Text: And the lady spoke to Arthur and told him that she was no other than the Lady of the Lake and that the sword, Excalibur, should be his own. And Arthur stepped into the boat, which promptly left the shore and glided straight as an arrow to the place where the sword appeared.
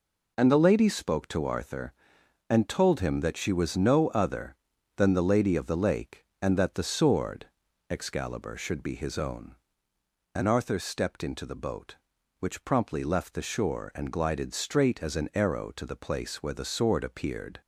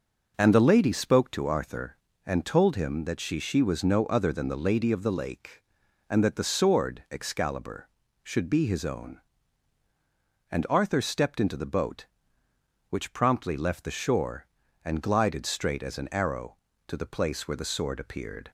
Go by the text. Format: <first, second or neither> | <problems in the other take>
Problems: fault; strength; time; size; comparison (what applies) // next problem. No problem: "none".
first | says "she" twice; at 3.3 s